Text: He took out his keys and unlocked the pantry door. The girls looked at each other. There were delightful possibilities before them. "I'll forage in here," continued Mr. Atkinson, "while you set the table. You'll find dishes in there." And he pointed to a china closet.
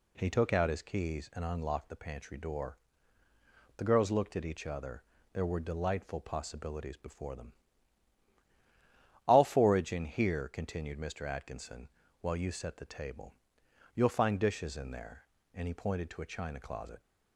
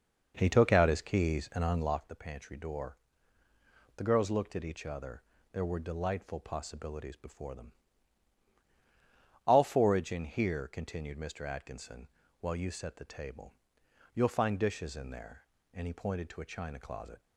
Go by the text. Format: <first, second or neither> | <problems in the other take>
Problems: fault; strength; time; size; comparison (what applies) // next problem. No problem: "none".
first | starts louder than the rest; noticeable; until 2.1 s; 6 dB